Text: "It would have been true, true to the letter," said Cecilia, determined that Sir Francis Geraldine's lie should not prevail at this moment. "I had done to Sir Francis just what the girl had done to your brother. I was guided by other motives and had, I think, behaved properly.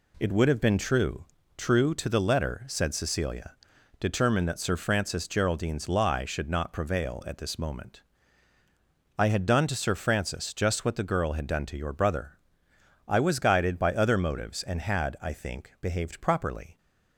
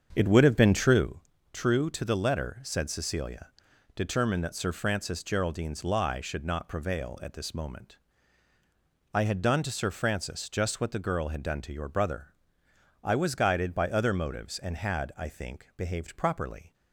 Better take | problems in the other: first | starts louder than the rest; until 1.1 s; 7 dB

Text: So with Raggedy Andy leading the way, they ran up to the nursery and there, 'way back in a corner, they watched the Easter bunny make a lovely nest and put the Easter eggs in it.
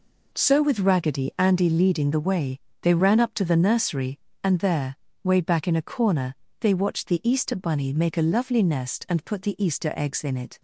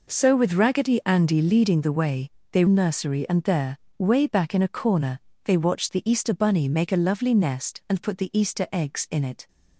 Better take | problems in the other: first | skips "ran up to the"; at 2.6 s

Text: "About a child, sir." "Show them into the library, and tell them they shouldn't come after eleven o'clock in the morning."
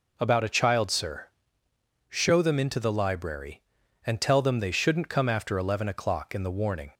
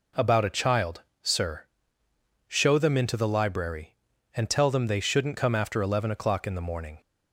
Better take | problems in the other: second | says "warning" for "morning"; at 6.5 s

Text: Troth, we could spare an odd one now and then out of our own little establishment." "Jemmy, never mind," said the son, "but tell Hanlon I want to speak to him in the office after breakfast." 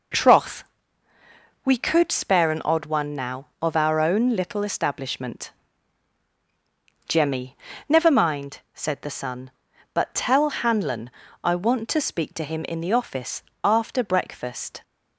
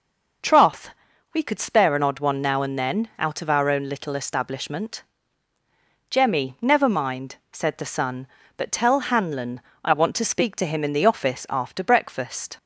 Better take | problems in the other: second | skips "and then out"; at 3.5 s // pauses between "Hanlon" and "I"; slight; at 11.0 s; 0.34 s long; slight in the second // pauses between "office" and "after"; slight; at 13.4 s; 0.24 s long

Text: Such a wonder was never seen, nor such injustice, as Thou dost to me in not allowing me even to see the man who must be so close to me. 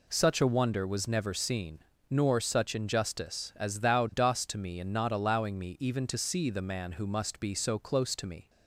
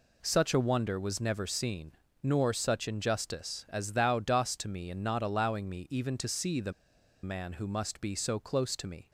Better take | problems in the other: first | pauses between "the" and "man"; noticeable; at 6.7 s; 0.51 s long

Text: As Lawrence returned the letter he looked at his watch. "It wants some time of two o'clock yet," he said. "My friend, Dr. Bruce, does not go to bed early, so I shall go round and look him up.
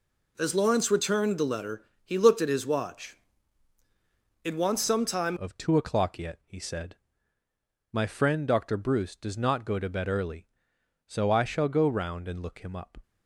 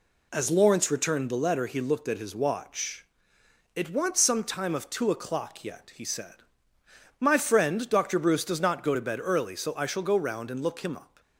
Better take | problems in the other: second | pauses between "letter" and "he"; slight; at 1.8 s; 0.20 s long // changes voice at "of"; from 5.3 s on; 7.6 s long

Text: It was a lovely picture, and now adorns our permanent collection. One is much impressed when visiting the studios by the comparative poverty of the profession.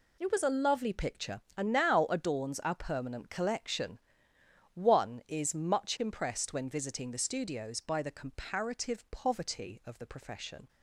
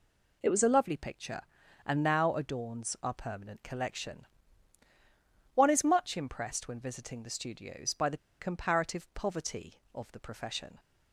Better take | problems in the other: first | pauses between "the" and "comparative"; slight; at 8.1 s; 0.21 s long

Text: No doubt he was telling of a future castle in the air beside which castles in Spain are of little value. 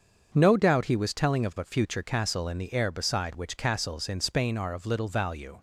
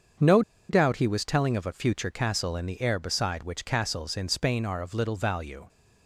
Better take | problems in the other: first | starts louder than the rest; until 1.5 s; 6.5 dB; also in the first // pauses between "No" and "doubt"; slight; at 0.4 s; 0.28 s long

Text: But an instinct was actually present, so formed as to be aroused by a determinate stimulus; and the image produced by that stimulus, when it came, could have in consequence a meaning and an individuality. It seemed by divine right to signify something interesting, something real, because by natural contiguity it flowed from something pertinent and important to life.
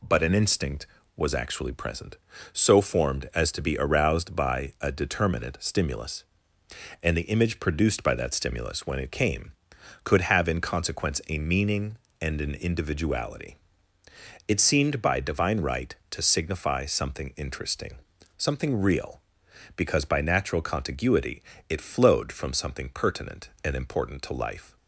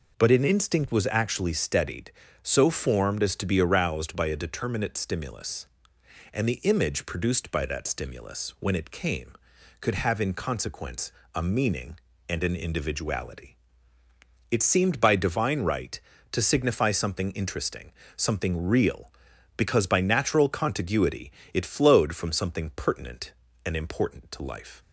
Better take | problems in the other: first | says "steadied" for "present"; at 1.5 s // pauses between "consequence" and "a"; slight; at 11.1 s; 0.24 s long // pauses between "contiguity" and "it"; slight; at 21.3 s; 0.20 s long; slight in the first

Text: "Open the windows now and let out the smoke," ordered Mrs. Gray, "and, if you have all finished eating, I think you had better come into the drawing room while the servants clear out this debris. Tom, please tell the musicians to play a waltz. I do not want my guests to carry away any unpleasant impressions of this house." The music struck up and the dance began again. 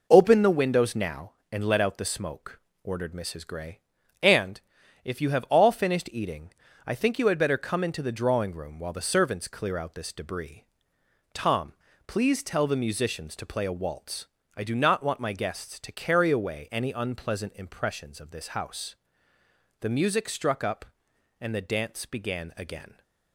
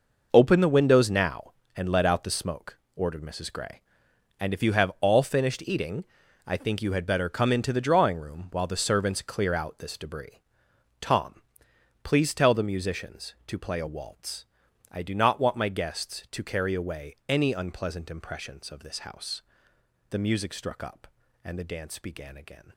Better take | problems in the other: first | gets quieter; strong; throughout; 11 dB

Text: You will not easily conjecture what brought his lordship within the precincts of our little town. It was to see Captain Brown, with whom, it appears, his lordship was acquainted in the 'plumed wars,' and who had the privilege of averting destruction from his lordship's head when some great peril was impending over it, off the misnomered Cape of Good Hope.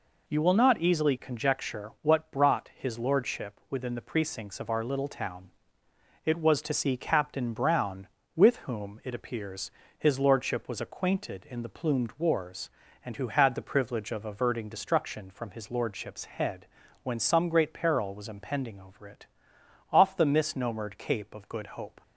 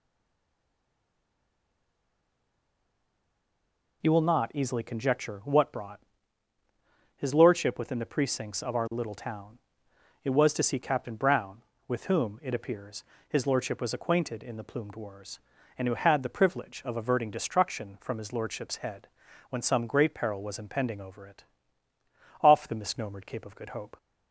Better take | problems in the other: first | stays silent before the first word; strong; until 4.0 s; 4.0 s long // pauses between "brought" and "his"; at 5.9 s; 1.1 s long // pauses between "head" and "when"; at 19.0 s; 0.42 s long; also in the first

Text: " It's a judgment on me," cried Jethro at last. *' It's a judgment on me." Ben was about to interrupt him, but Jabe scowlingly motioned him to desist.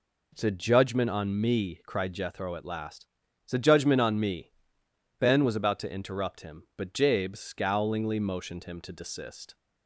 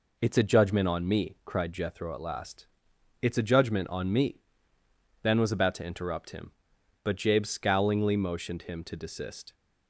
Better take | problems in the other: neither | none

